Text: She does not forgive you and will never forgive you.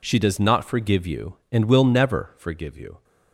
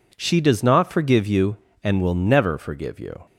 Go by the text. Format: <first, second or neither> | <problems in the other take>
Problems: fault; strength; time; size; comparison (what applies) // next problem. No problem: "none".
neither | none